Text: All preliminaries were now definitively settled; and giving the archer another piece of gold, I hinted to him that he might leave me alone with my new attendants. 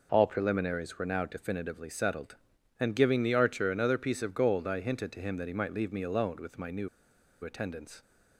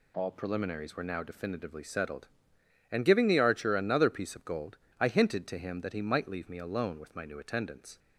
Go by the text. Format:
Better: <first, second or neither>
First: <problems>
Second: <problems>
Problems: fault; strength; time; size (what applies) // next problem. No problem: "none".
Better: second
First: pauses between "new" and "attendants"; noticeable; at 6.8 s; 0.54 s long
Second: none